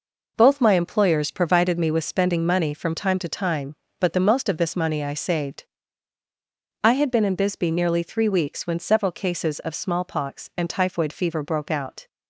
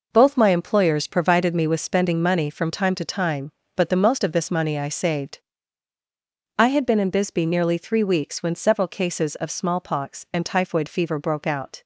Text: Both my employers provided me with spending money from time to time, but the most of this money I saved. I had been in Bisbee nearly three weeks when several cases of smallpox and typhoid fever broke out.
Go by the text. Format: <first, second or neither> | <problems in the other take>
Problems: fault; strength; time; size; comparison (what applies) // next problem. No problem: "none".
neither | none